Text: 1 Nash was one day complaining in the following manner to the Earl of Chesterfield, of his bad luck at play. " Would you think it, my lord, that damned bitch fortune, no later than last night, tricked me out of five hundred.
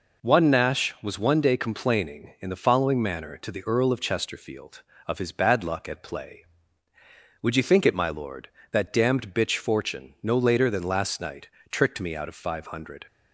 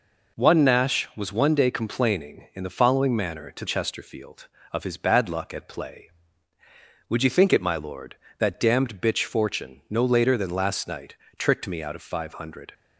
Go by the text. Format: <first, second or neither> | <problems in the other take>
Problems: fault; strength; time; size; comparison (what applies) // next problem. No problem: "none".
first | skips "the Earl of"; at 3.6 s